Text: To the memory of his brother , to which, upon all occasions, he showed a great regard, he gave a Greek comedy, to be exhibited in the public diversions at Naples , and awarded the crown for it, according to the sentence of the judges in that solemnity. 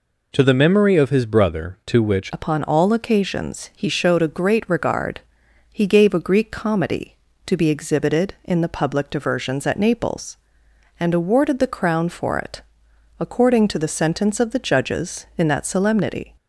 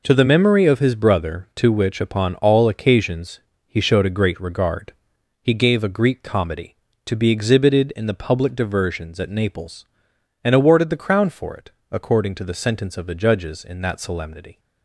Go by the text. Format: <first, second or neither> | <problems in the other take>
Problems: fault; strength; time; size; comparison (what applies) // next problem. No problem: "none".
second | changes voice at "upon"; from 2.3 s on; 14.0 s long